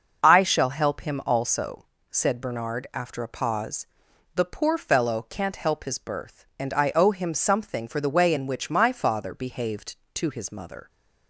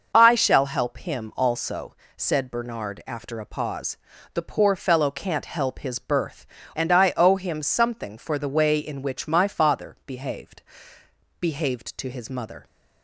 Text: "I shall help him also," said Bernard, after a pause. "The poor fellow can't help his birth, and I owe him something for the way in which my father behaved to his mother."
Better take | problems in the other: first | says "behaved" twice; at 11.3 s

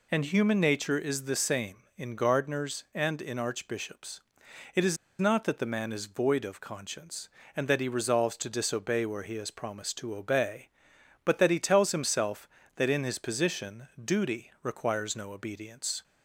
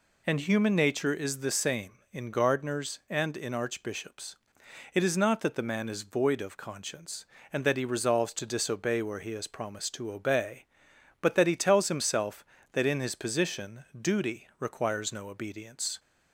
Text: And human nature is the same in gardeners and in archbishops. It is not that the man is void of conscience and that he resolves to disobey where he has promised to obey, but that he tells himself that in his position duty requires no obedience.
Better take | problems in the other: second | pauses between "is" and "not"; slight; at 4.9 s; 0.22 s long // pauses between "position" and "duty"; slight; at 13.8 s; 0.16 s long; slight in the second

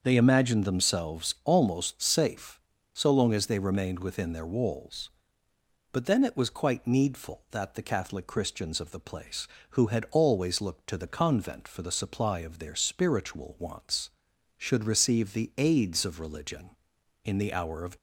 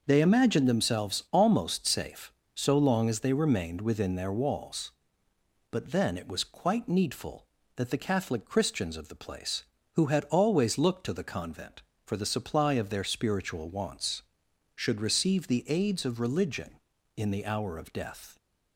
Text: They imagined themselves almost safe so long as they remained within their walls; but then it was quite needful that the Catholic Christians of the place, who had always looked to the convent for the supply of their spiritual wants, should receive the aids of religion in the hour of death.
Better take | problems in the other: second | starts louder than the rest; until 1.0 s; 6.5 dB // stops before "death"; at 17.9 s

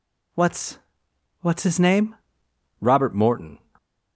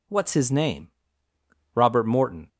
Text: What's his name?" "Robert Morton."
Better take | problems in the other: second | says "What's" twice; at 1.4 s

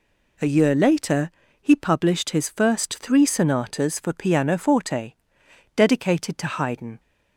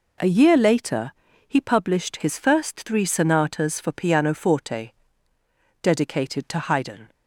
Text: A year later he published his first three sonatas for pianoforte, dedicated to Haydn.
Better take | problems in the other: neither | pauses between "later" and "he"; slight; the same in both

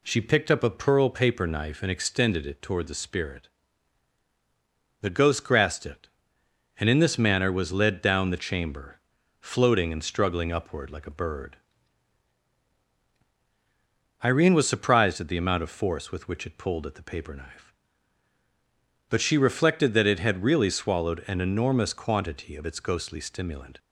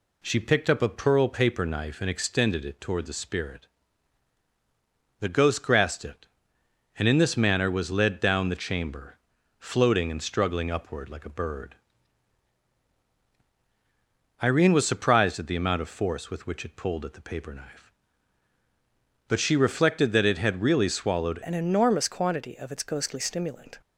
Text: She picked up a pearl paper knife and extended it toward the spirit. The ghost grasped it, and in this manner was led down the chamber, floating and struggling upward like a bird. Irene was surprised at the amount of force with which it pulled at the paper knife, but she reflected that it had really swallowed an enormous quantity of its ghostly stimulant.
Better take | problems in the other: first | changes voice at "an"; from 21.4 s on; 2.3 s long

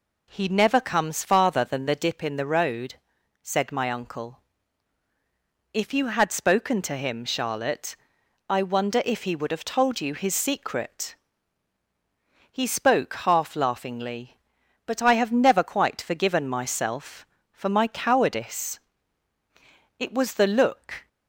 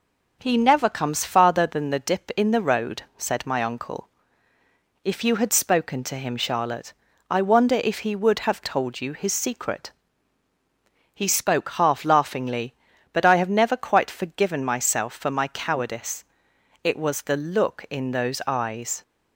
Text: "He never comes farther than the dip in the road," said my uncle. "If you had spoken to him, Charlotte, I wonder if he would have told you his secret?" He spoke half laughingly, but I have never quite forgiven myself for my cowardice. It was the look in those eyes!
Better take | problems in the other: second | stops before "in those eyes"; at 21.0 s

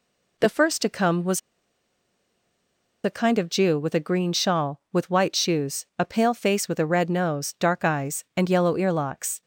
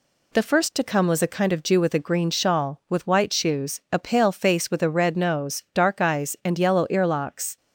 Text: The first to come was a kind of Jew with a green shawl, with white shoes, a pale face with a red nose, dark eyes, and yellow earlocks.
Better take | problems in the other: second | pauses between "was" and "a"; strong; at 1.3 s; 1.6 s long

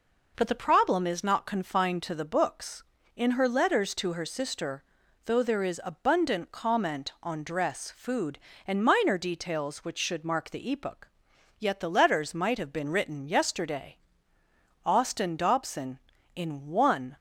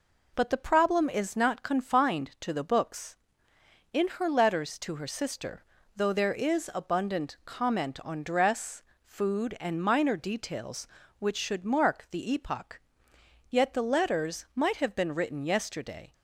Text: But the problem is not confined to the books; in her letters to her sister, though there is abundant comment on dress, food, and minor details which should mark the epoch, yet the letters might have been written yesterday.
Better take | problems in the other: second | goes on to say "Austin Dobson in one"; strong; from 14.8 s on; 2.3 s long

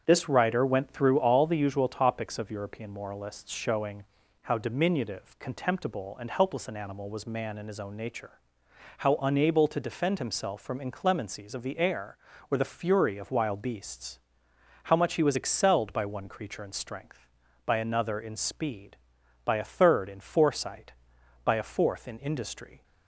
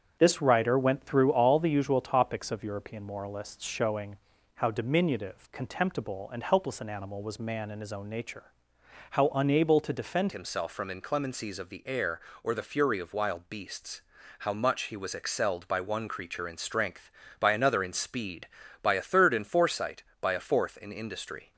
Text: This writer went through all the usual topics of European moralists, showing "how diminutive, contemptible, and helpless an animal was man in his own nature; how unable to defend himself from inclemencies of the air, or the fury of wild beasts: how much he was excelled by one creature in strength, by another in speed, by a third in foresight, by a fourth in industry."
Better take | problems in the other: first | starts louder than the rest; strong; until 1.2 s; 7.5 dB; strong in the first // pauses between "showing" and "how"; at 4.1 s; 0.38 s long; also in the first // changes voice at "himself"; from 10.3 s on; 11.2 s long

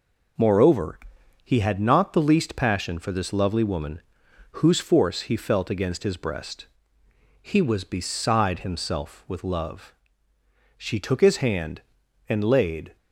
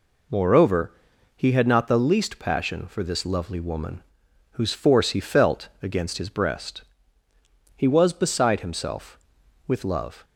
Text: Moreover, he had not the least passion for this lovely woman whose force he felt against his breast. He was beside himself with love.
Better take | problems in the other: second | pauses between "woman" and "whose"; noticeable; at 4.0 s; 0.50 s long; noticeable in the second // goes on to say "She took his hand and laid"; strong; from 10.7 s on; 2.1 s long

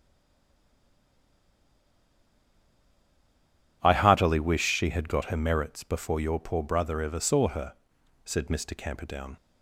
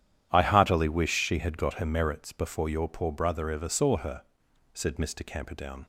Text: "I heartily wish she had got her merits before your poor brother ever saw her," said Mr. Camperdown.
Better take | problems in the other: second | stays silent before the first word; strong; until 3.8 s; 3.8 s long // starts louder than the rest; strong; until 4.8 s; 10.5 dB; strong in the second

